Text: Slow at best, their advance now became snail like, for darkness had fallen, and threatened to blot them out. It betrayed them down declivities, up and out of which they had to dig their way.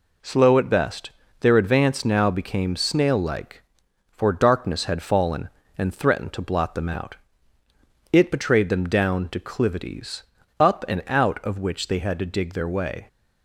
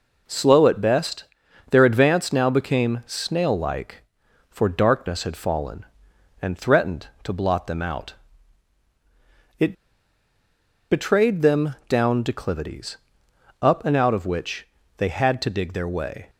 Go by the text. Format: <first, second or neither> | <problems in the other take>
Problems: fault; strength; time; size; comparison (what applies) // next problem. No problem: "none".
first | pauses between "It" and "betrayed"; at 9.7 s; 1.1 s long // pauses between "which" and "they"; slight; at 14.6 s; 0.30 s long